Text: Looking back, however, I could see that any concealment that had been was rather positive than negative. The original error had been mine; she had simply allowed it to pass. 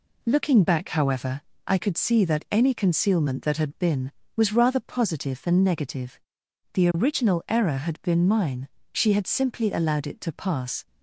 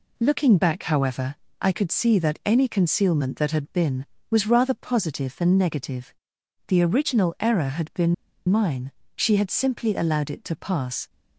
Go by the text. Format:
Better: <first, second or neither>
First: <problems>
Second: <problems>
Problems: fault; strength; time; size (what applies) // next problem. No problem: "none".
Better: first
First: none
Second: pauses between "been" and "mine"; slight; at 8.1 s; 0.34 s long